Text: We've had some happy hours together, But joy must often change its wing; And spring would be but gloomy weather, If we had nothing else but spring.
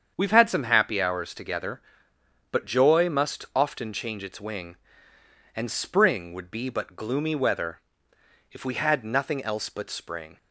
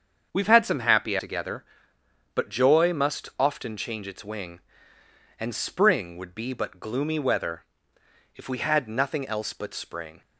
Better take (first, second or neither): first